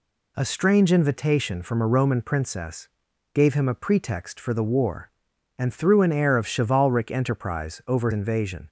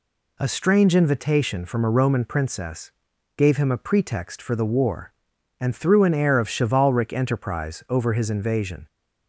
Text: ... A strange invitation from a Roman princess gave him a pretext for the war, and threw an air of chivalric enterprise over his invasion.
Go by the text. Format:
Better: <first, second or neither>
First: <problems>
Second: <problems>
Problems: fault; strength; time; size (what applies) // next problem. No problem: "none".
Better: second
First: pauses between "princess" and "gave"; at 2.8 s; 0.44 s long // skips "his"; at 8.1 s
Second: pauses between "princess" and "gave"; at 2.9 s; 0.44 s long